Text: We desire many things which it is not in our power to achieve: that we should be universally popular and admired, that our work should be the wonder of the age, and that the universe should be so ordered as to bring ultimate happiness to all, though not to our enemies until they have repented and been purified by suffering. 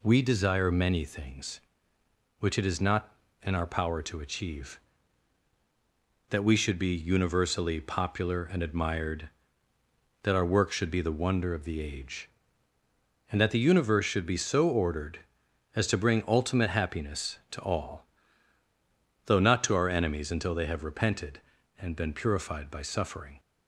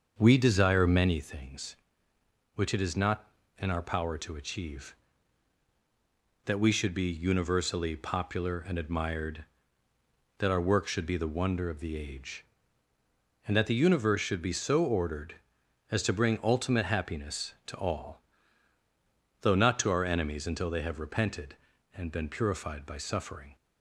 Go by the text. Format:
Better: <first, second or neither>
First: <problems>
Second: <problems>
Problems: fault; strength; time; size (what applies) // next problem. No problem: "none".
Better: first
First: none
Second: starts louder than the rest; until 1.3 s; 6.5 dB